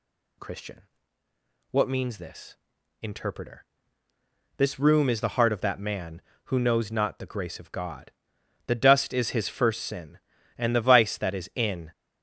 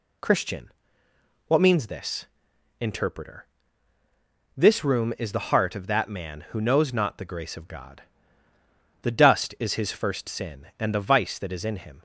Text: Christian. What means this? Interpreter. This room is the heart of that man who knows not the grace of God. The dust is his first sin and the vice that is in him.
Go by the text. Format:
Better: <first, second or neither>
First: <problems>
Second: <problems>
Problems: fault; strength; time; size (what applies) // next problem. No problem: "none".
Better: second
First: stops before "him"; at 11.9 s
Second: none